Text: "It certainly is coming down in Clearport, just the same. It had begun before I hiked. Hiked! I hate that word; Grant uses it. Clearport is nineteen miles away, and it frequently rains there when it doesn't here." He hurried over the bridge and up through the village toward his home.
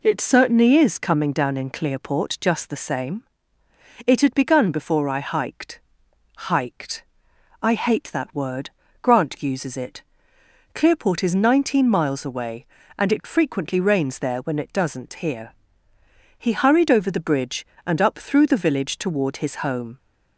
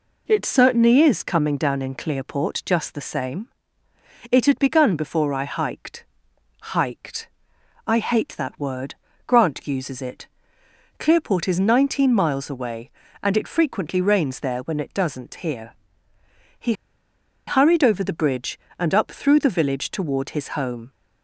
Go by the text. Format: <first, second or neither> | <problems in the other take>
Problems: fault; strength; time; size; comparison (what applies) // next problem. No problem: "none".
first | pauses between "He" and "hurried"; noticeable; at 16.7 s; 0.74 s long